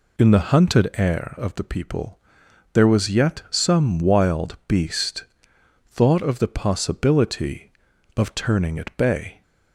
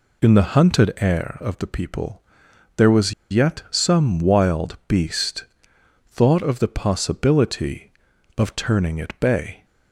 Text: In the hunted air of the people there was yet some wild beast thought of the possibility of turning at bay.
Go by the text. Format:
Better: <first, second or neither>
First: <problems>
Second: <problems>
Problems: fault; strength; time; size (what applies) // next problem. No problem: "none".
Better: first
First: pauses between "people" and "there"; noticeable; at 2.1 s; 0.56 s long // pauses between "beast" and "thought"; noticeable; at 5.2 s; 0.64 s long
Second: pauses between "people" and "there"; noticeable; at 2.2 s; 0.56 s long // pauses between "was" and "yet"; slight; at 3.1 s; 0.17 s long // pauses between "beast" and "thought"; noticeable; at 5.4 s; 0.64 s long